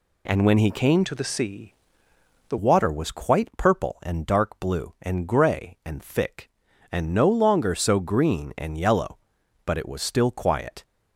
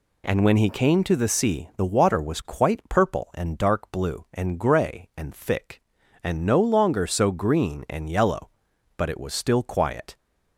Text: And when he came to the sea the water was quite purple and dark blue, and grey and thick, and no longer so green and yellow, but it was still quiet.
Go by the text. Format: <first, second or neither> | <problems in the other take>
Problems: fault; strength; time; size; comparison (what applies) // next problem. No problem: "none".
second | changes voice from "to" to "the"; from 1.0 to 2.5 s; 1.5 s long // pauses between "sea" and "the"; noticeable; at 1.7 s; 0.80 s long